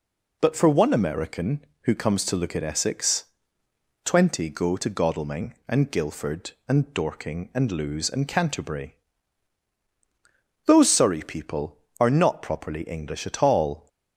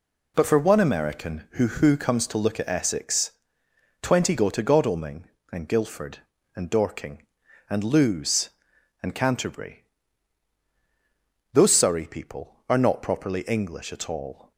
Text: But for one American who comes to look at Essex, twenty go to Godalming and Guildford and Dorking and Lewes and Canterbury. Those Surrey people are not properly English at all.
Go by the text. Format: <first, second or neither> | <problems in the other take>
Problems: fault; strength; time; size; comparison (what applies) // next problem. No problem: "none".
first | says "who" twice; at 1.6 s